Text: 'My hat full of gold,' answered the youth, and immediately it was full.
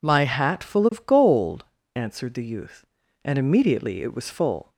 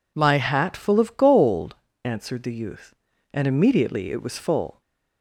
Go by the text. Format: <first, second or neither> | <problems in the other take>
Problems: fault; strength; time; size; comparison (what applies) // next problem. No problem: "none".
neither | none